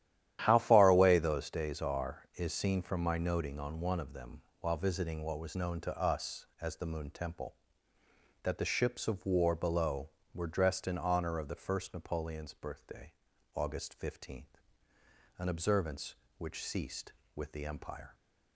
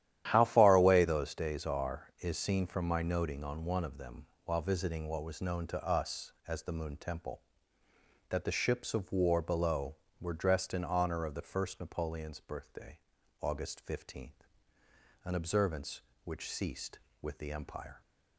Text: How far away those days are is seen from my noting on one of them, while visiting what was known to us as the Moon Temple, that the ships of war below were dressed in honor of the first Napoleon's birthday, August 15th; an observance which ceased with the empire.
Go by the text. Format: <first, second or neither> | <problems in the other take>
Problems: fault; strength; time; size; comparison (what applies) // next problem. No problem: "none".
neither | starts louder than the rest; strong; the same in both